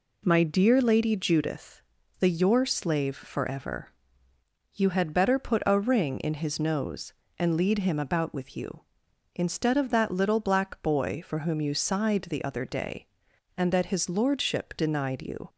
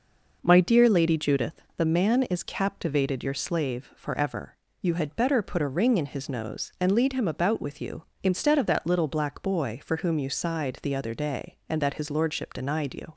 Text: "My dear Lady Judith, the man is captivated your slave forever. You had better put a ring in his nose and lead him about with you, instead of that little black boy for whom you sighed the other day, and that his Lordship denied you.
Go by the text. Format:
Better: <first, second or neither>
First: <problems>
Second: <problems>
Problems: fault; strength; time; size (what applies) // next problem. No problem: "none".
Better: second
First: skips "man is captivated"; at 2.2 s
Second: none